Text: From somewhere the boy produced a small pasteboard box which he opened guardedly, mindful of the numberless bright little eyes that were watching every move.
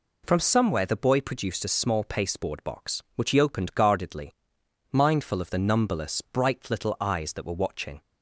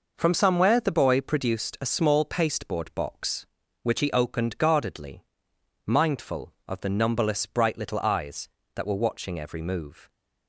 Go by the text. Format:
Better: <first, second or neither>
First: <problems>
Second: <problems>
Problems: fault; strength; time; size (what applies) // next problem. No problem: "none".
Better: second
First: stops before "every move"; at 8.0 s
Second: none